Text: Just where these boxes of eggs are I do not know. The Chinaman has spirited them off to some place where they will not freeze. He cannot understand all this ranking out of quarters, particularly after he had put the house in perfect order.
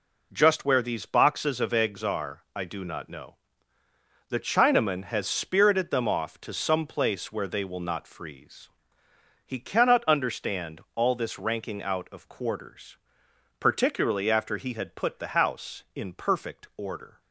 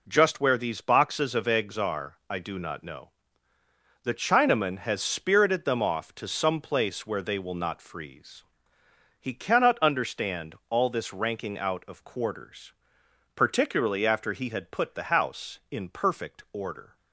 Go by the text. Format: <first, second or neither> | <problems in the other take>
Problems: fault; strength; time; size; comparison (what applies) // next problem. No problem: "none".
neither | none